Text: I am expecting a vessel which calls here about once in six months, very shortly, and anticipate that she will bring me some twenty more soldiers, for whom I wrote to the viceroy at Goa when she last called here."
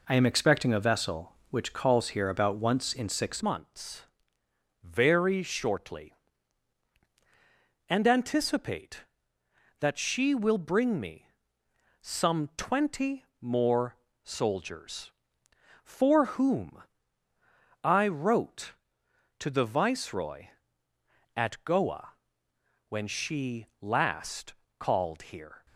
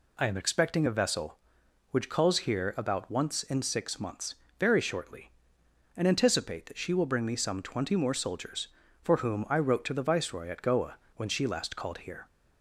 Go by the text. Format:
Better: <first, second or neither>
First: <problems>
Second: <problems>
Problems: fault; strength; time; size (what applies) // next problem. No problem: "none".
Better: second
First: changes voice at "months"; from 3.4 s on; 22.2 s long // pauses between "me" and "some"; noticeable; at 11.2 s; 0.74 s long // pauses between "twenty" and "more"; slight; at 13.2 s; 0.16 s long // pauses between "more" and "soldiers"; slight; at 13.9 s; 0.26 s long // pauses between "whom" and "I"; at 16.8 s; 1.0 s long // pauses between "Goa" and "when"; noticeable; at 22.1 s; 0.74 s long // pauses between "she" and "last"; slight; at 23.6 s; 0.16 s long // pauses between "last" and "called"; slight; at 24.5 s; 0.24 s long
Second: pauses between "Goa" and "when"; slight; at 10.9 s; 0.20 s long